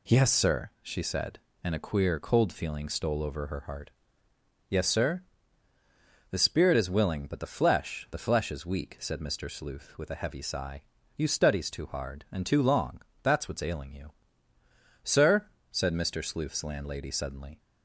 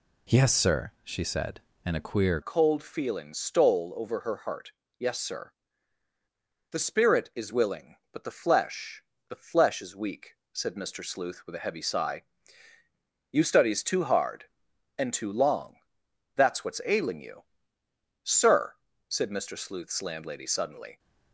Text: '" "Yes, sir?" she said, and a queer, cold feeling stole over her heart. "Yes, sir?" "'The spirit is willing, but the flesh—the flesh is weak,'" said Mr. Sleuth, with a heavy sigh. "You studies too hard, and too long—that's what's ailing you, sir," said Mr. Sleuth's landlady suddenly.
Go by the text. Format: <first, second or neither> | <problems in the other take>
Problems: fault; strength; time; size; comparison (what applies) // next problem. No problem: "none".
first | changes voice at "cold"; from 2.4 s on; 18.5 s long